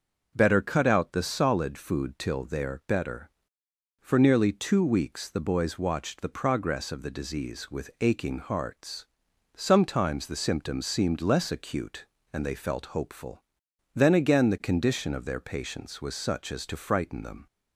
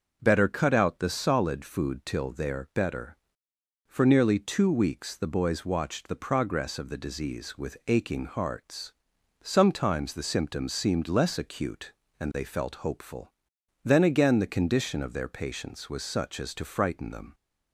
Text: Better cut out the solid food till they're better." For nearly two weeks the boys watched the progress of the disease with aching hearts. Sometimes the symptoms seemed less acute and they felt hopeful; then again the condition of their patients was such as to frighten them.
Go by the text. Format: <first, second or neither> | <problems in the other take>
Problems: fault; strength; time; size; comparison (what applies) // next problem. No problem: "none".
neither | none